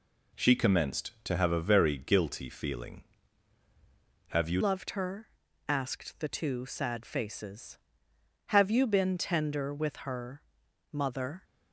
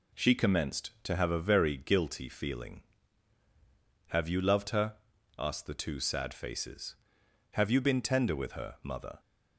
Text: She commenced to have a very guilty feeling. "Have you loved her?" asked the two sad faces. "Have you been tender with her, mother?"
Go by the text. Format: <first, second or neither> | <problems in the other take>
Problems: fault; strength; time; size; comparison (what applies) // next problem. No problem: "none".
second | changes voice at "loved"; from 4.6 s on; 6.8 s long